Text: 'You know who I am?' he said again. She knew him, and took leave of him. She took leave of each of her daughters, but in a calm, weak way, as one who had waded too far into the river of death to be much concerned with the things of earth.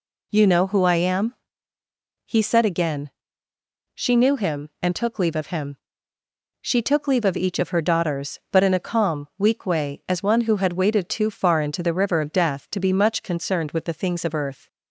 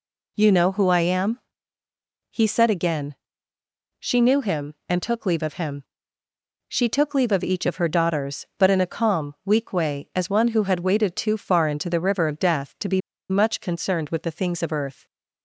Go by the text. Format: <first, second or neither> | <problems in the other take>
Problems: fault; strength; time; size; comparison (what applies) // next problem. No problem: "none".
first | pauses between "be" and "much"; slight; at 13.0 s; 0.29 s long